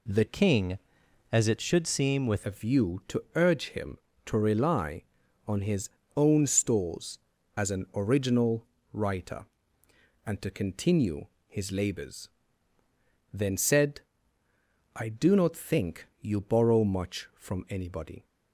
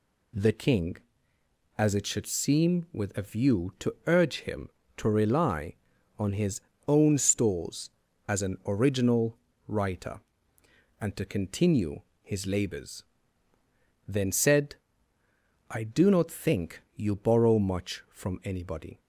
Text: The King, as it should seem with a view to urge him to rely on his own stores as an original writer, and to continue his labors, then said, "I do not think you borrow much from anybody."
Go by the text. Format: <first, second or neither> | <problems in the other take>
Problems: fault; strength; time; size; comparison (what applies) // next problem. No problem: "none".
second | changes voice from "King" to "with"; from 0.2 to 2.4 s; 2.2 s long // pauses between "his" and "own"; slight; at 5.8 s; 0.28 s long; slight in the second // pauses between "original" and "writer"; slight; at 8.6 s; 0.26 s long; slight in the second // pauses between "continue" and "his"; slight; at 11.2 s; 0.20 s long; slight in the second